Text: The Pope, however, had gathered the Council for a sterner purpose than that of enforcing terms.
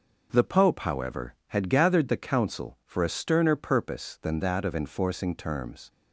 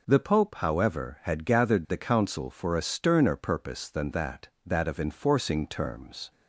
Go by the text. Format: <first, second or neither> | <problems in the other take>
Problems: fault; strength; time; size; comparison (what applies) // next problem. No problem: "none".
first | says "that" twice; at 4.6 s